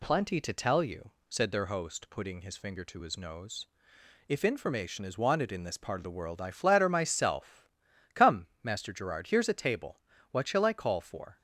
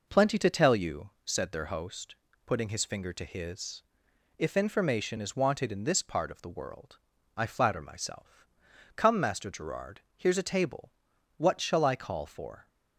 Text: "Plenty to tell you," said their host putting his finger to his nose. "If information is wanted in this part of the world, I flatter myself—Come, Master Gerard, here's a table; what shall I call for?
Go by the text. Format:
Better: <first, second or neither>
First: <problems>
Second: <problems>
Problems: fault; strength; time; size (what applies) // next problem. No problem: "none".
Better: first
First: none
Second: pauses between "host" and "putting"; slight; at 2.1 s; 0.32 s long // skips "nose"; at 4.1 s